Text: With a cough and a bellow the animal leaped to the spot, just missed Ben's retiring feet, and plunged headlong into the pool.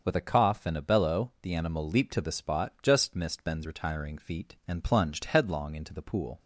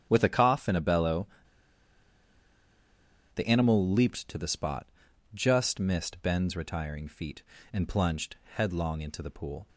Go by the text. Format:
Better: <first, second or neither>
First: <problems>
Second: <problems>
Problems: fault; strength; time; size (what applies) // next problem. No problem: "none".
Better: first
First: starts louder than the rest; until 1.0 s; 6.5 dB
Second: starts louder than the rest; strong; until 1.1 s; 10 dB // pauses between "bellow" and "the"; strong; at 1.2 s; 2.0 s long